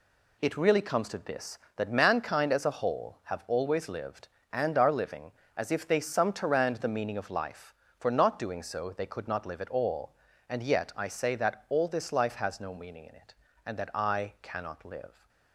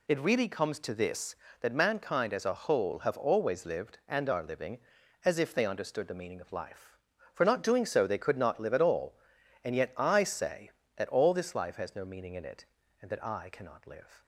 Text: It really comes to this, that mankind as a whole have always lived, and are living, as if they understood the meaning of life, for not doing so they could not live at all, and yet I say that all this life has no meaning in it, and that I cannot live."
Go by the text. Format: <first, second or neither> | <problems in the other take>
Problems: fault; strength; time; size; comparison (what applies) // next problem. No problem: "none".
second | says "sumterand" for "understood"; at 5.9 s